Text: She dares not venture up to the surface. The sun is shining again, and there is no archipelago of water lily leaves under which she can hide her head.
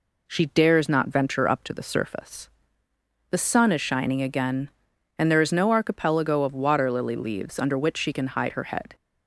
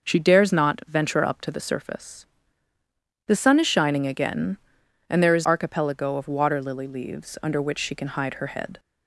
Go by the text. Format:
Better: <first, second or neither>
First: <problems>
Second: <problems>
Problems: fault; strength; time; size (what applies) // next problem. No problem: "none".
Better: first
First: none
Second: skips "no"; at 5.4 s